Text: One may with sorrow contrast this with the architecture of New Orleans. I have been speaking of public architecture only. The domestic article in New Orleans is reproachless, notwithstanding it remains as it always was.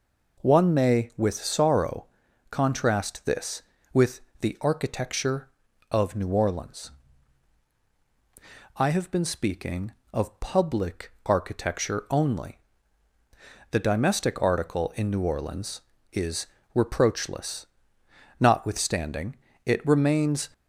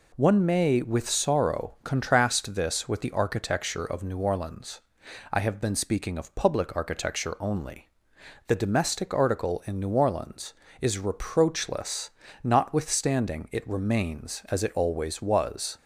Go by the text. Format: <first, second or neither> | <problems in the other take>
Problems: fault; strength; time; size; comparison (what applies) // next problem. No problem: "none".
second | pauses between "sorrow" and "contrast"; at 2.0 s; 0.44 s long // pauses between "with" and "the"; slight; at 4.2 s; 0.18 s long // pauses between "public" and "architecture"; slight; at 11.1 s; 0.16 s long // pauses between "is" and "reproachless"; slight; at 16.4 s; 0.16 s long // pauses between "notwithstanding" and "it"; slight; at 19.3 s; 0.30 s long // stops before "as it always was"; at 20.5 s